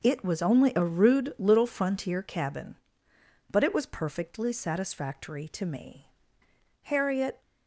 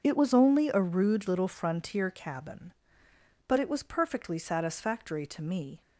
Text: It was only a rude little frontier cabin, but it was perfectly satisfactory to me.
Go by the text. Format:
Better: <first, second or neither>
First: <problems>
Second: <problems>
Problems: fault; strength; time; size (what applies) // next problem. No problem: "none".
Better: second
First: goes on to say "Harriet"; from 6.8 s on; 0.58 s long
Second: none